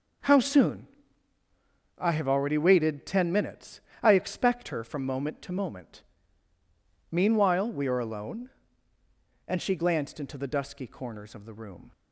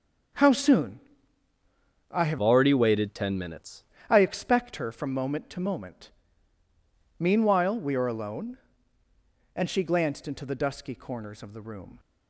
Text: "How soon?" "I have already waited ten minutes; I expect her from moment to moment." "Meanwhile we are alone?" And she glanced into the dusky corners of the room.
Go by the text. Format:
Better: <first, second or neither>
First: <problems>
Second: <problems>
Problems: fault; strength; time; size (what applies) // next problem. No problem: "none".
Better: first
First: starts louder than the rest; noticeable; until 2.3 s; 6 dB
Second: starts louder than the rest; until 2.5 s; 6.5 dB // changes voice from "already" to "minutes"; from 2.4 to 3.8 s; 1.4 s long